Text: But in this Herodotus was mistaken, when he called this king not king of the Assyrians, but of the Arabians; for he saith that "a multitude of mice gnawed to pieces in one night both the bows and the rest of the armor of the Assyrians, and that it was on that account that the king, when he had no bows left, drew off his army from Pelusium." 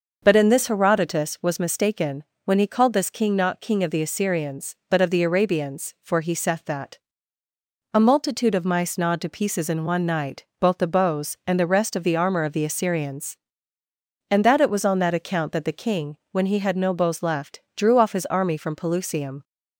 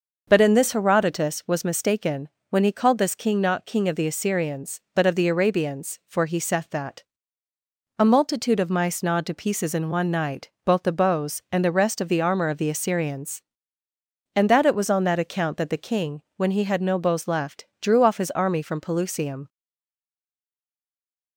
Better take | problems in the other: first | starts louder than the rest; noticeable; until 1.2 s; 6 dB; noticeable in the first // pauses between "that" and "a"; noticeable; at 7.0 s; 0.96 s long; noticeable in the first // pauses between "night" and "both"; slight; at 10.5 s; 0.16 s long; slight in the first // stays silent after the last word; noticeable; from 19.4 s on; 1.9 s long

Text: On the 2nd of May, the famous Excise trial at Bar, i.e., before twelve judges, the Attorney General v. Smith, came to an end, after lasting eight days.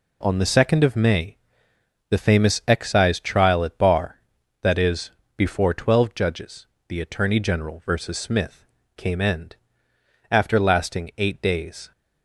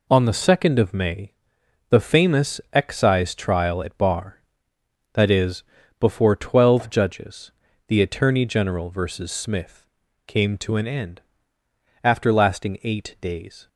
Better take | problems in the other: second | skips "to an"; at 9.1 s

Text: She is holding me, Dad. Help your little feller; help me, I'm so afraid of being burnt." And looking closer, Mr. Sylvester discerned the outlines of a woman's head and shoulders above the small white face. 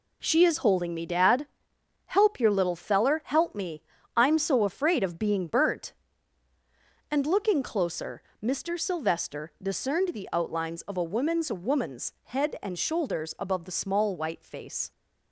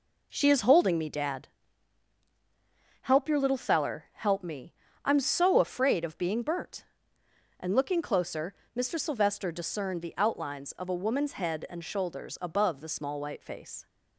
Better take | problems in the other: second | says "woman's" twice; at 11.5 s

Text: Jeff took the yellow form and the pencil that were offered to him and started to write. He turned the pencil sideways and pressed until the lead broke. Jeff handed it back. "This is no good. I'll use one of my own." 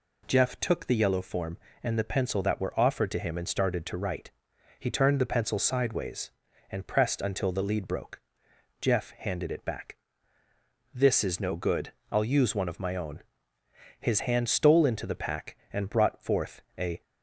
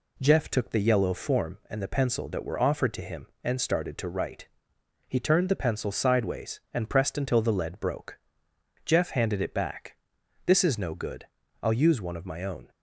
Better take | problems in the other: second | goes on to say "His hand stole into the pack and brought forth a"; strong; from 14.0 s on; 3.0 s long

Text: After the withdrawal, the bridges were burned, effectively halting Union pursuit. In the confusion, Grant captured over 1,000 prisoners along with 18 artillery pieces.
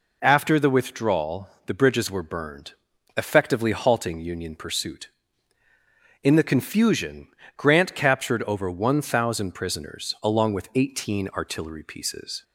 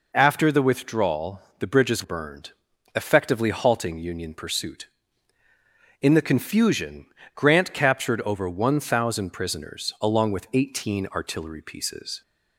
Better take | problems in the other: first | skips "were"; at 2.0 s

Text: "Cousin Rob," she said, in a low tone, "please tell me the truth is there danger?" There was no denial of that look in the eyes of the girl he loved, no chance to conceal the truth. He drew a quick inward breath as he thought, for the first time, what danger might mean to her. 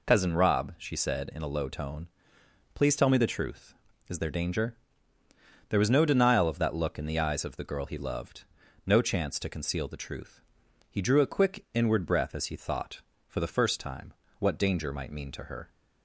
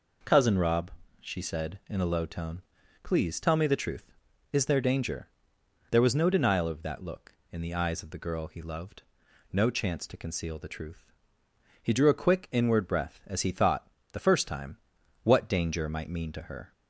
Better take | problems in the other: first | skips "for"; at 13.9 s

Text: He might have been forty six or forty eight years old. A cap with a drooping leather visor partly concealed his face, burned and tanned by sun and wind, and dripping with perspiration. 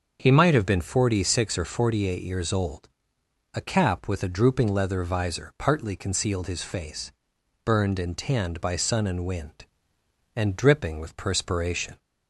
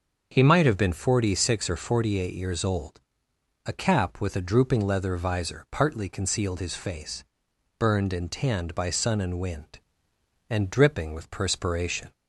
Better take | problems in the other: neither | starts louder than the rest; the same in both

